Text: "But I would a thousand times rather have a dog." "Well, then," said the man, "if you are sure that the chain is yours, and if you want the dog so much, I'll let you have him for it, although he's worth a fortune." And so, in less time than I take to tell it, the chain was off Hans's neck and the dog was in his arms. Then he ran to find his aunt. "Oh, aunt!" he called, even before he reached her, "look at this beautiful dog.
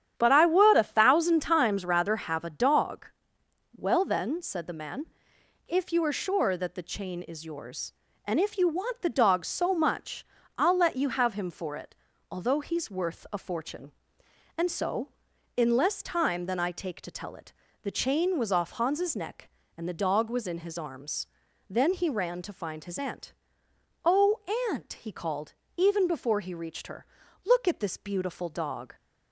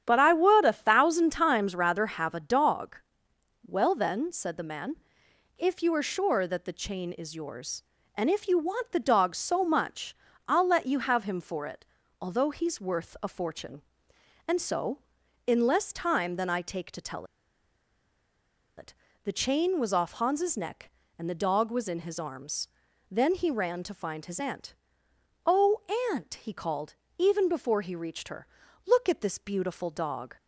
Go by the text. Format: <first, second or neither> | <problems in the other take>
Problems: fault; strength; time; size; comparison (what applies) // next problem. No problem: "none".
first | starts louder than the rest; strong; until 1.0 s; 9.5 dB; strong in the first // pauses between "tell" and "it"; strong; at 17.2 s; 1.5 s long